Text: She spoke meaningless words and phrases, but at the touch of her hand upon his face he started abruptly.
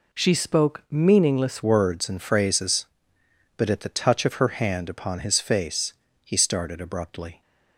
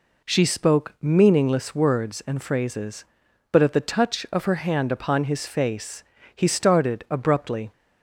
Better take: second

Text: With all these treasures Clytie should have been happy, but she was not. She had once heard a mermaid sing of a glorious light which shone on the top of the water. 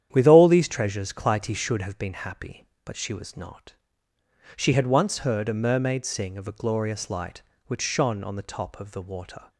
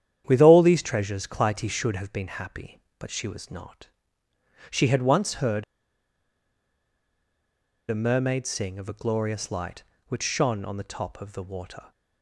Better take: first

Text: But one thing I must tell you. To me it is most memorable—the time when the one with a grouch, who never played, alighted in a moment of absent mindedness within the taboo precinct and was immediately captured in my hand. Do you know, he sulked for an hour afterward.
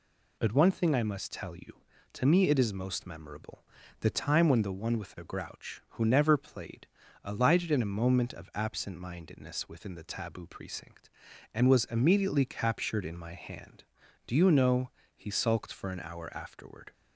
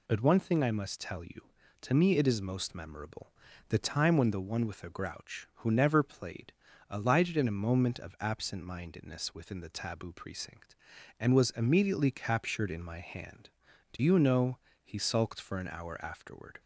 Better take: neither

